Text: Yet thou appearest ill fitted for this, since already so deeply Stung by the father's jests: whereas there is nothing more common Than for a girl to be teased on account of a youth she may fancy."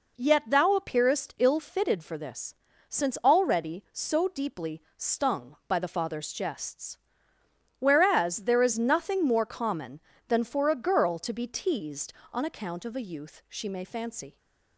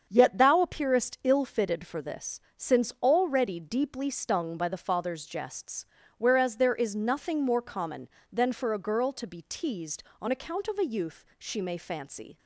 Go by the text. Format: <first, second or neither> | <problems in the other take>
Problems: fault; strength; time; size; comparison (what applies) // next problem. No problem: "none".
first | starts louder than the rest; strong; until 1.1 s; 7 dB // skips "so"; at 3.5 s